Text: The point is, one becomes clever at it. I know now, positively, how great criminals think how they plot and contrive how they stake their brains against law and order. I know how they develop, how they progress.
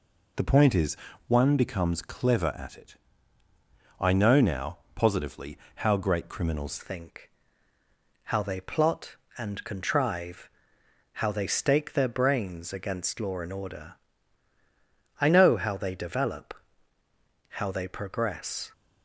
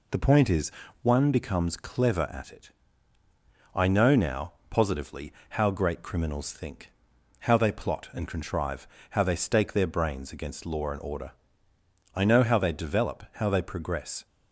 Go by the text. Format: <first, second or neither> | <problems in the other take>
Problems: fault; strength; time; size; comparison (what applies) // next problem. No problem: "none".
second | changes voice at "think"; from 6.7 s on; 12.0 s long // pauses between "think" and "how"; noticeable; at 7.2 s; 0.96 s long; noticeable in the second // pauses between "contrive" and "how"; noticeable; at 10.4 s; 0.66 s long; slight in the second